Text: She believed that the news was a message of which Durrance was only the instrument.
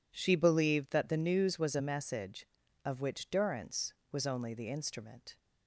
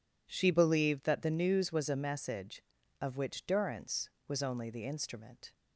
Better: neither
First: none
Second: none

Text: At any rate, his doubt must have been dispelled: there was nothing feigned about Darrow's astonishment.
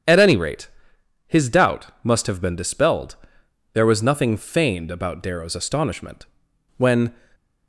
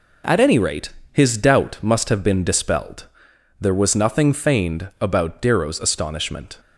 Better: second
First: starts louder than the rest; strong; until 1.6 s; 8.5 dB // pauses between "doubt" and "must"; slight; at 1.8 s; 0.16 s long // goes on to say "When"; slight; from 6.7 s on; 0.38 s long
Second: none

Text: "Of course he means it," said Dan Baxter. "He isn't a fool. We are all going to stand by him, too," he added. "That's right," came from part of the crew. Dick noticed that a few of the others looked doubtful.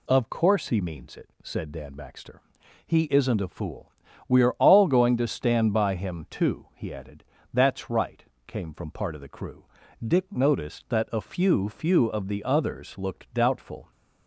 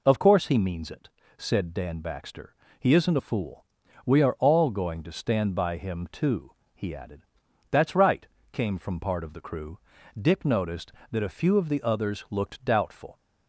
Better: second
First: says "few" twice; at 11.6 s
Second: none

